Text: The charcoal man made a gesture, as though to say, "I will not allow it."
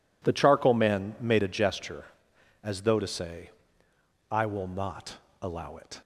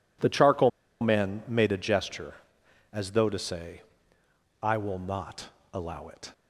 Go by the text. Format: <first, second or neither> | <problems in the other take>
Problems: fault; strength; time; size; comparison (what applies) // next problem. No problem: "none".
first | pauses between "charcoal" and "man"; slight; at 0.6 s; 0.31 s long // pauses between "not" and "allow"; slight; at 5.4 s; 0.24 s long; slight in the first